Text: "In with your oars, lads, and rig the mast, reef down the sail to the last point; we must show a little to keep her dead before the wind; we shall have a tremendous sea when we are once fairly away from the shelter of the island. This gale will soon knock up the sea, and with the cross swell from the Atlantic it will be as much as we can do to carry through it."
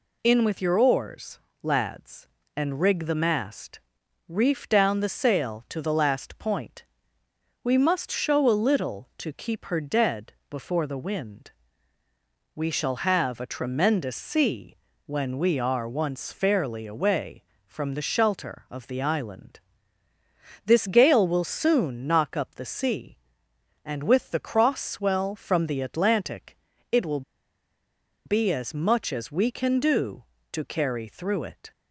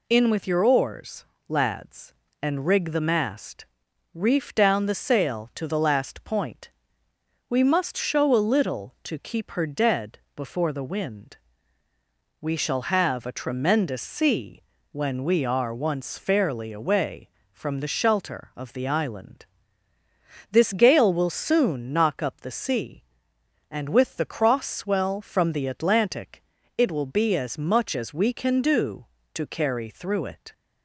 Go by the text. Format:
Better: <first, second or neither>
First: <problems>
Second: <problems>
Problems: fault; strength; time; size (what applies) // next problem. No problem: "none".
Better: second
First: pauses between "dead" and "before"; slight; at 10.3 s; 0.16 s long // pauses between "sea" and "when"; slight; at 14.7 s; 0.30 s long // pauses between "Atlantic" and "it"; slight; at 26.5 s; 0.34 s long // pauses between "will" and "be"; at 27.2 s; 1.0 s long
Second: pauses between "dead" and "before"; slight; at 10.1 s; 0.16 s long // pauses between "sea" and "when"; slight; at 14.6 s; 0.30 s long // pauses between "Atlantic" and "it"; slight; at 26.4 s; 0.34 s long